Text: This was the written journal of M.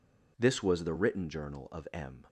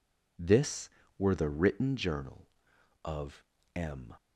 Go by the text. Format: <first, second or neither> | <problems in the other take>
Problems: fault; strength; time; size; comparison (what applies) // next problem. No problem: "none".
first | says "were" for "was"; at 1.1 s // pauses between "of" and "M"; slight; at 3.4 s; 0.32 s long